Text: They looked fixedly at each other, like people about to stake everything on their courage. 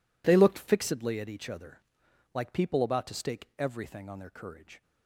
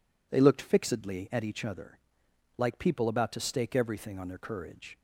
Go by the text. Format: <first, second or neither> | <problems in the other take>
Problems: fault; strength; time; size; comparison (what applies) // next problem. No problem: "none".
second | gets quieter; strong; throughout; 14.5 dB